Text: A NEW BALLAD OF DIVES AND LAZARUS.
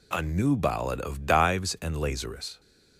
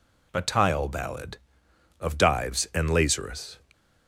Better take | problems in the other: first | says "Tile" for "NEW"; at 0.4 s

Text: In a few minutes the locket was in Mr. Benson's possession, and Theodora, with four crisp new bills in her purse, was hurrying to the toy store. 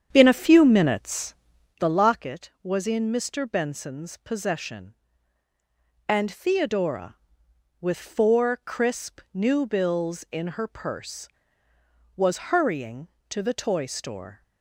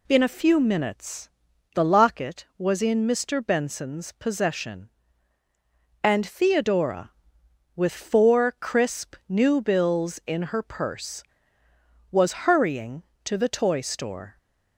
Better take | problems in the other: second | starts louder than the rest; strong; until 1.9 s; 8.5 dB // pauses between "minutes" and "the"; at 1.3 s; 0.44 s long; also in the second

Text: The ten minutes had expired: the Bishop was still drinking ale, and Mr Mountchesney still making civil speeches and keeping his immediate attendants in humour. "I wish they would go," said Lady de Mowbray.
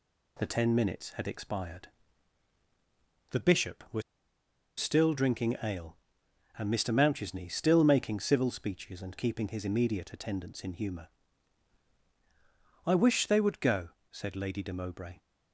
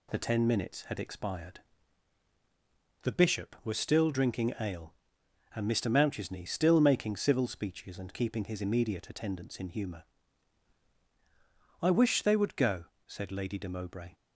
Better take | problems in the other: second | pauses between "was" and "still"; noticeable; at 4.0 s; 0.77 s long

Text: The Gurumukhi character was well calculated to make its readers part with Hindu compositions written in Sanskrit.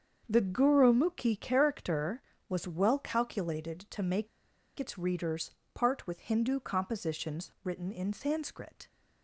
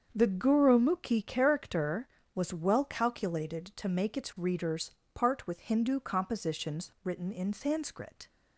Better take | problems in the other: second | starts louder than the rest; until 1.2 s; 7 dB; also in the second // pauses between "make" and "its"; noticeable; at 4.2 s; 0.51 s long // pauses between "readers" and "part"; slight; at 5.5 s; 0.24 s long; slight in the second

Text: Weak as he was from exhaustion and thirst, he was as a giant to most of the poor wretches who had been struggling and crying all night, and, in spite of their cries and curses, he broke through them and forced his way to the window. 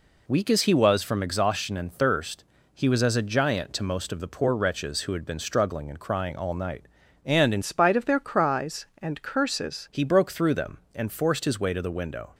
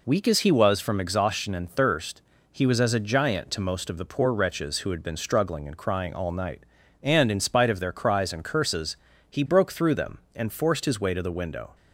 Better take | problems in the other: second | changes voice from "spite" to "curses"; from 7.6 to 9.8 s; 2.2 s long

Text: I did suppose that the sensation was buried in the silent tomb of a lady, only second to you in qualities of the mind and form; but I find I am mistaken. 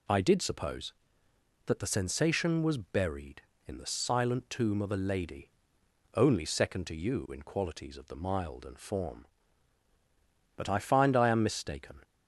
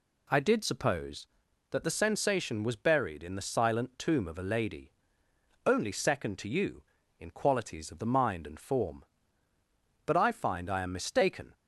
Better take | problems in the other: second | says "mild" for "mind"; at 8.1 s

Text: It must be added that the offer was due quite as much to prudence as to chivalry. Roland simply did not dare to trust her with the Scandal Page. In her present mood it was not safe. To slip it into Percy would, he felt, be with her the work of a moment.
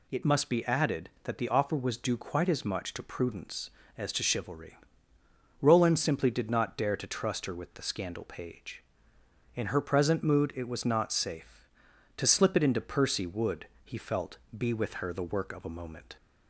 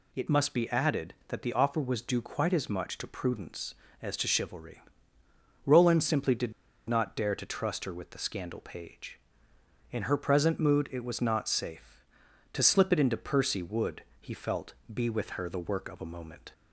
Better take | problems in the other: first | pauses between "did" and "not"; slight; at 6.5 s; 0.35 s long

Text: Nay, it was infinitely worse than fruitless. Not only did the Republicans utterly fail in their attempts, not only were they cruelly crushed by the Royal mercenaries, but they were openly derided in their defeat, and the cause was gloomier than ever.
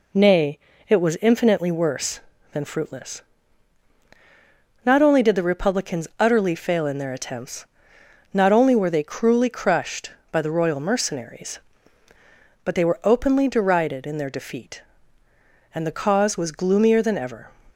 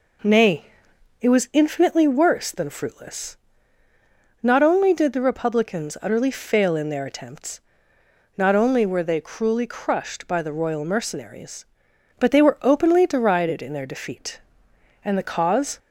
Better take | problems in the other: first | stops before "was gloomier than ever"; at 15.7 s

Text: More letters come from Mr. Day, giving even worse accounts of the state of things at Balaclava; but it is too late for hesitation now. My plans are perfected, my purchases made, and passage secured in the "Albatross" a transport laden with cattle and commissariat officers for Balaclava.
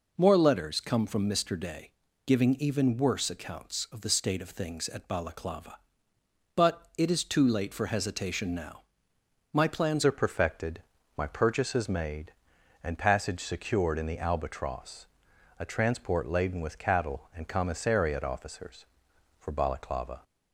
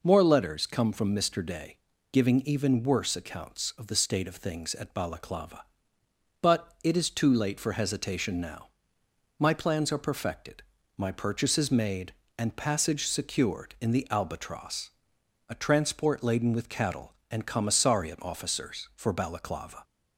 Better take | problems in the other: second | changes voice at "are"; from 10.0 s on; 10.2 s long // pauses between "Albatross" and "a"; noticeable; at 15.0 s; 0.54 s long; noticeable in the second

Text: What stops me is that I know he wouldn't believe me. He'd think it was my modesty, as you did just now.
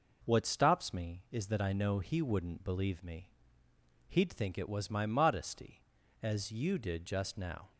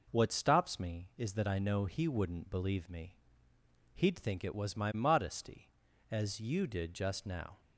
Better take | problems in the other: neither | none

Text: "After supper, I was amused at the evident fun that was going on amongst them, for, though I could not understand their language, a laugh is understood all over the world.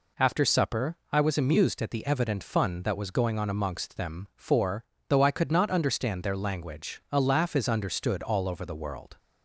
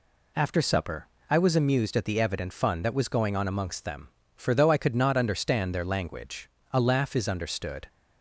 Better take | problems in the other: first | stops before "all over the world"; at 7.8 s

